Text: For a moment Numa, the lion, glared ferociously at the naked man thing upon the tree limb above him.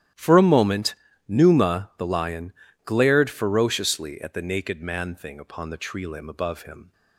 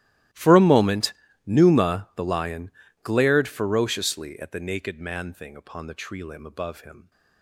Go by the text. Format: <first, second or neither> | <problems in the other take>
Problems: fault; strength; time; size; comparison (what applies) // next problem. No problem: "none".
first | gets quieter; strong; throughout; 23 dB // starts louder than the rest; strong; until 1.6 s; 14.5 dB; strong in the first // pauses between "moment" and "Numa"; slight; at 1.1 s; 0.32 s long; slight in the first